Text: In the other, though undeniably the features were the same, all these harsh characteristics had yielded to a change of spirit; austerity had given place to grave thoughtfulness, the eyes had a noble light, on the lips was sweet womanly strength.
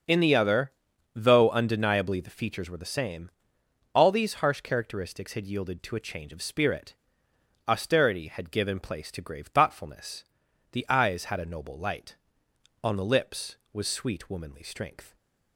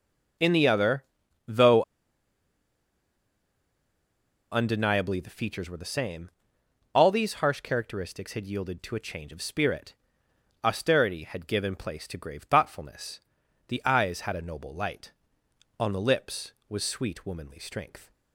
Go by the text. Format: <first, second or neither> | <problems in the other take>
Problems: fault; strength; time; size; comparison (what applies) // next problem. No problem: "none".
first | starts louder than the rest; until 1.8 s; 6.5 dB; also in the first // pauses between "though" and "undeniably"; strong; at 1.8 s; 2.7 s long